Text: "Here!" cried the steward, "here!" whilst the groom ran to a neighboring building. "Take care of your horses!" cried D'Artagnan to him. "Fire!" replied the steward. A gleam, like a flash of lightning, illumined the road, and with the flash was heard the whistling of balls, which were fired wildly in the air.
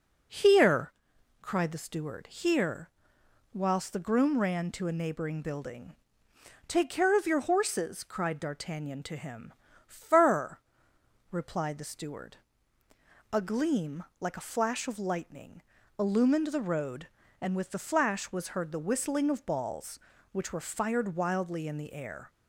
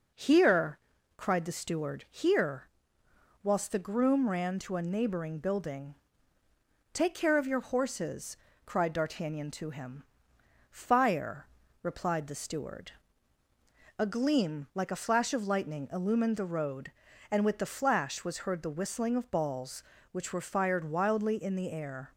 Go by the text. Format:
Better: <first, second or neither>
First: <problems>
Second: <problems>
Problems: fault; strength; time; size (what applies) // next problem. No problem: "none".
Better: second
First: says "Fur" for "Fire"; at 9.8 s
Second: none